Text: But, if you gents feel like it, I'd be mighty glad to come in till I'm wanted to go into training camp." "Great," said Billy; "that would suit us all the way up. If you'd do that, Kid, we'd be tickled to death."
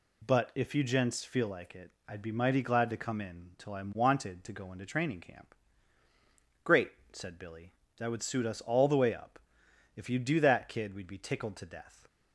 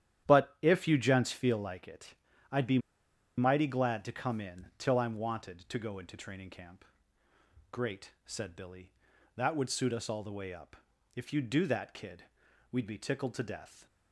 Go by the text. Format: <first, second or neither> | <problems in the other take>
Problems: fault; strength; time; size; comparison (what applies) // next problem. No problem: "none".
first | starts louder than the rest; strong; until 1.3 s; 11 dB // pauses between "be" and "mighty"; noticeable; at 2.7 s; 0.58 s long